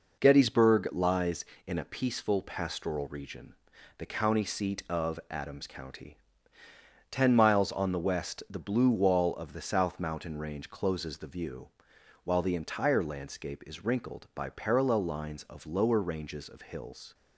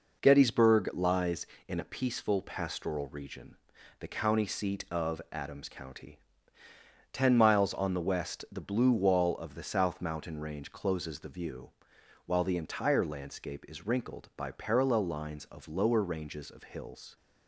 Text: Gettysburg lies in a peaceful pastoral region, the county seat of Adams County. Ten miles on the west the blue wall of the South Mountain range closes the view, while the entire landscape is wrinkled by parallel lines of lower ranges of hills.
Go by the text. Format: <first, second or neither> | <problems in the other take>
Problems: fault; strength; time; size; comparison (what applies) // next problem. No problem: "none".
neither | none